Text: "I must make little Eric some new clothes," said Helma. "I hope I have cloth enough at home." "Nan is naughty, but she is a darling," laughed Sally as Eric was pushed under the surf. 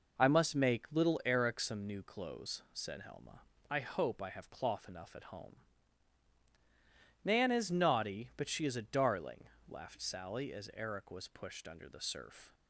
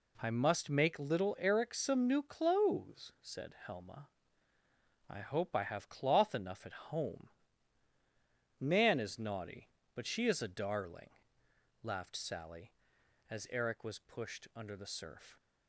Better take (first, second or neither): neither